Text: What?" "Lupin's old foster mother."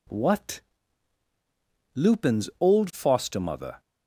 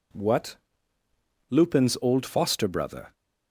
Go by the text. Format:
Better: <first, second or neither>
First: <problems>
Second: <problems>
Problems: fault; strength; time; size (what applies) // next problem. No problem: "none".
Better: first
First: none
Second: says "brother" for "mother"; at 2.6 s